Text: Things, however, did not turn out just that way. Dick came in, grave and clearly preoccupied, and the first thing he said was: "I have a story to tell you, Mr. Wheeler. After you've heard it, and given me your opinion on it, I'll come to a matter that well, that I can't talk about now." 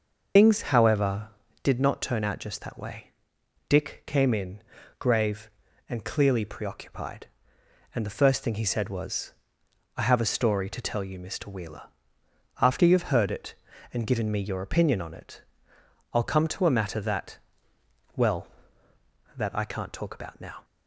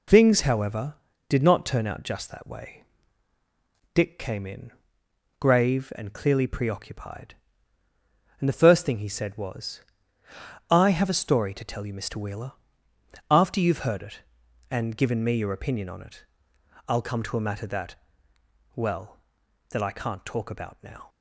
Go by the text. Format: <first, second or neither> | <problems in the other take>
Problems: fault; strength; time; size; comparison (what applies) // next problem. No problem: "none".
second | loses the start of "Things"; at 0.3 s; 120 ms // pauses between "that" and "well"; noticeable; at 17.3 s; 0.80 s long; noticeable in the second